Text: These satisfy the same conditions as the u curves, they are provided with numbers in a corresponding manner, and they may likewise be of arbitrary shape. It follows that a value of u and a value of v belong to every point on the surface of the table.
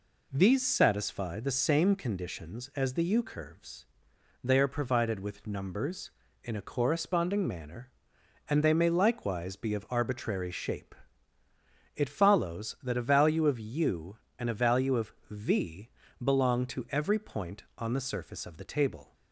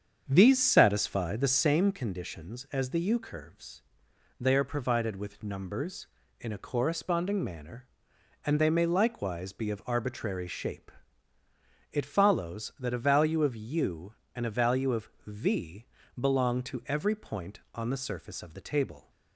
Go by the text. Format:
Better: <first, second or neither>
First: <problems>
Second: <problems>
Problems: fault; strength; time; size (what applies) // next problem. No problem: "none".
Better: first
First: pauses between "of" and "v"; slight; at 15.1 s; 0.16 s long // pauses between "v" and "belong"; slight; at 15.8 s; 0.34 s long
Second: starts louder than the rest; strong; until 1.7 s; 7.5 dB // pauses between "of" and "v"; slight; at 15.0 s; 0.16 s long // pauses between "v" and "belong"; slight; at 15.8 s; 0.34 s long